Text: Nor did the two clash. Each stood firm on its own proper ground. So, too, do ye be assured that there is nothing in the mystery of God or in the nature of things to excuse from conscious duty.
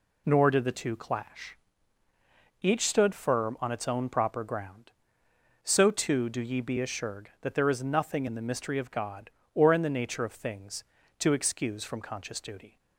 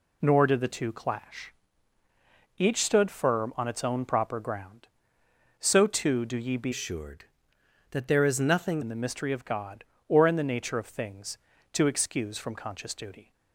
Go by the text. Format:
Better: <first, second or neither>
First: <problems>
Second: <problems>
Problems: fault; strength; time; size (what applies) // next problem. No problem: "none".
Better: first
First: none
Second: changes voice from "assured" to "nothing"; from 6.7 to 8.8 s; 2.1 s long